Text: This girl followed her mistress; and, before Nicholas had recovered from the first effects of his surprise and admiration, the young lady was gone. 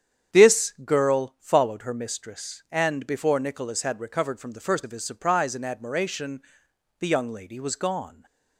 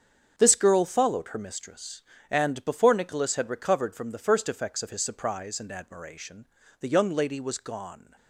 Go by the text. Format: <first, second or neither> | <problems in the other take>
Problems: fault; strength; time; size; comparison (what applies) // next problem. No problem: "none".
second | starts louder than the rest; strong; until 1.4 s; 8.5 dB; strong in the second // skips "effects"; at 4.8 s // stays silent after the last word; slight; from 8.0 s on; 0.5 s long